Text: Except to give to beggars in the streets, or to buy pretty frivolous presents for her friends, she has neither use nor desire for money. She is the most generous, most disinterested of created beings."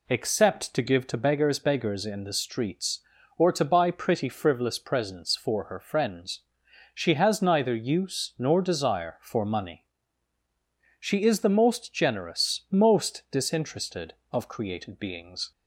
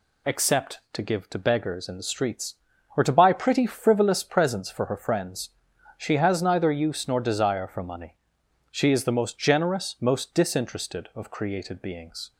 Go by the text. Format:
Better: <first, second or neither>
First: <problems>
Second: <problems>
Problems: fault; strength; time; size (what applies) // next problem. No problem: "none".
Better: second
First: says "beggars" twice; at 1.5 s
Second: none